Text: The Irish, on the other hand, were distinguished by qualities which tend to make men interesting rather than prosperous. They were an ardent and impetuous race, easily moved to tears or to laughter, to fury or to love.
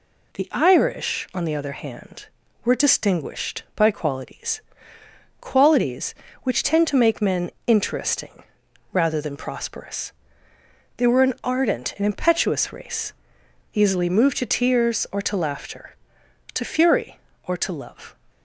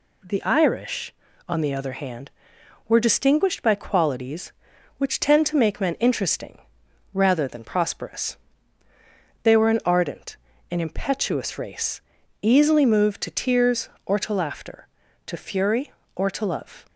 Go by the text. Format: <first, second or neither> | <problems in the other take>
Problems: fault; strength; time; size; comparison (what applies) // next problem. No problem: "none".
second | says "qualities" twice; at 5.3 s // pauses between "men" and "interesting"; slight; at 7.4 s; 0.16 s long // pauses between "interesting" and "rather"; noticeable; at 8.4 s; 0.48 s long; noticeable in the second